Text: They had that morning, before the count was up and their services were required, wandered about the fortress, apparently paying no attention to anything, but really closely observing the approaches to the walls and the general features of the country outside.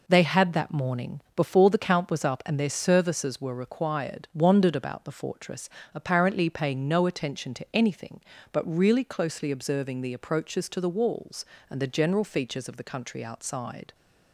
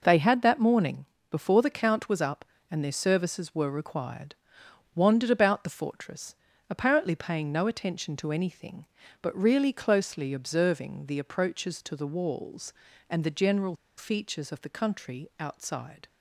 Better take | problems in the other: first | pauses between "general" and "features"; slight; at 13.7 s; 0.22 s long

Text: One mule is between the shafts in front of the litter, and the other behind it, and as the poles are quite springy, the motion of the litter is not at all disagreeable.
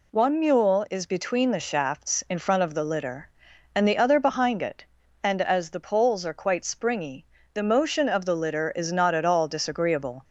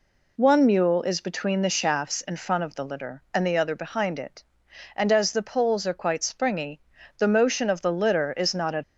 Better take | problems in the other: first | stops before "all disagreeable"; at 8.8 s

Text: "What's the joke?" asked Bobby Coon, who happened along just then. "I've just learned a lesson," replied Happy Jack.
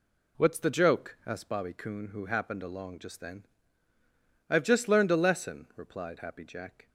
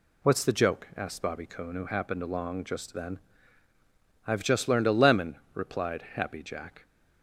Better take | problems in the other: first | says "lemon" for "lesson"; at 4.9 s

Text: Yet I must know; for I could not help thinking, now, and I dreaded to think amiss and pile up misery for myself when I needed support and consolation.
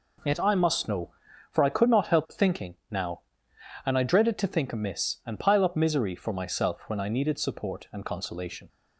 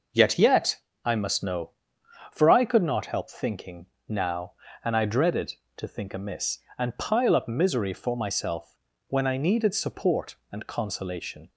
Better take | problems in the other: first | says "Yet" twice; at 0.3 s // pauses between "myself" and "when"; slight; at 8.7 s; 0.32 s long

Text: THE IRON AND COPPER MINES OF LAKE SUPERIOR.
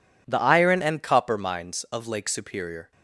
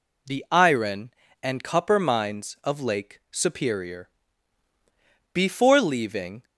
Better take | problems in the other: first | goes on to say "BEFORE leaving"; noticeable; from 5.3 s on; 1.1 s long

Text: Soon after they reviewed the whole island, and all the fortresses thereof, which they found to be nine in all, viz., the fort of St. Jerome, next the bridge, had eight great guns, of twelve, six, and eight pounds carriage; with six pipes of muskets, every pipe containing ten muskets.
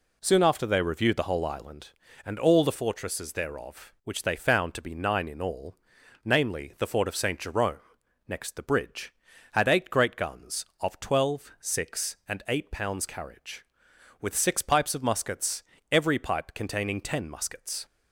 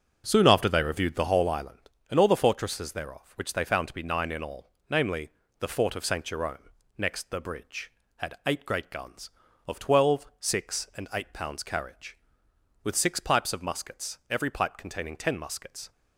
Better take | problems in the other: first | starts louder than the rest; until 1.6 s; 7 dB

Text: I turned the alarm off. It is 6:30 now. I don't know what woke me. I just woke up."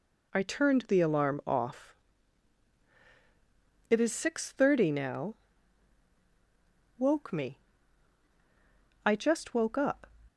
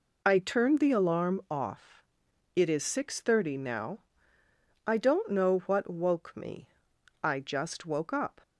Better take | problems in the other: second | skips "I don't know what"; at 6.1 s

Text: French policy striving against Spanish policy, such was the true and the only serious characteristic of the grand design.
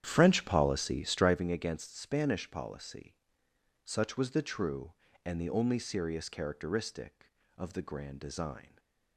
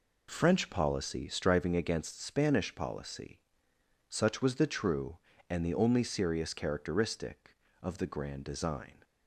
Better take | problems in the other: second | starts louder than the rest; strong; until 1.5 s; 10 dB // stays silent after the last word; slight; from 8.6 s on; 0.5 s long

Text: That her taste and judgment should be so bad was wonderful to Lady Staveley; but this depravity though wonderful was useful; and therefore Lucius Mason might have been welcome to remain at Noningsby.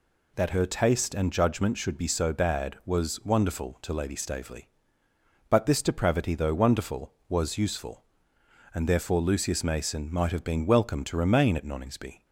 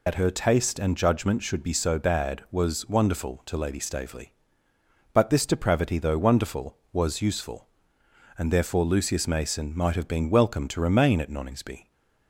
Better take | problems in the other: first | loses the start of "That"; at 0.0 s; 60 ms

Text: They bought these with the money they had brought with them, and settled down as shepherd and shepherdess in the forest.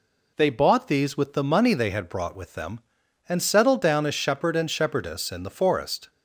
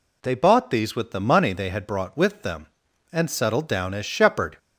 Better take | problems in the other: first | stops before "and shepherdess in the forest"; at 4.5 s

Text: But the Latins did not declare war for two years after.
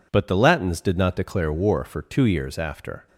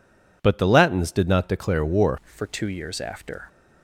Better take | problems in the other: first | changes voice at "for"; from 2.3 s on; 1.1 s long

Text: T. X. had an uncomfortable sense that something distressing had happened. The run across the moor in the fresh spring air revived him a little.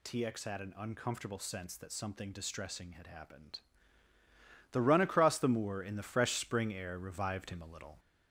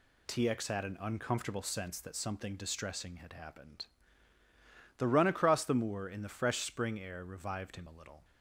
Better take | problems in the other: second | gets louder; slight; throughout; 2.5 dB

